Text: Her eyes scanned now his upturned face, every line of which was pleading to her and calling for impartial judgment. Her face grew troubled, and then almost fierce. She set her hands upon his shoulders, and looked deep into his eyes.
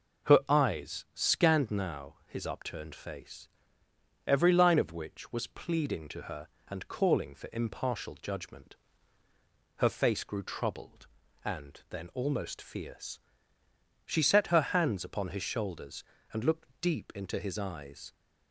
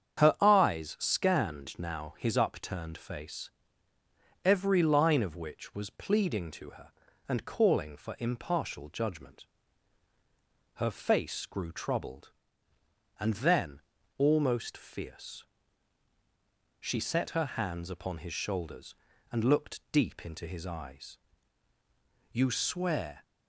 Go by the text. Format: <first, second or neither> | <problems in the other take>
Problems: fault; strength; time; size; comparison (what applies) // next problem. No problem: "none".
first | starts louder than the rest; strong; until 1.2 s; 8 dB // pauses between "then" and "almost"; slight; at 13.8 s; 0.36 s long // goes on to say "You swear"; noticeable; from 22.3 s on; 0.90 s long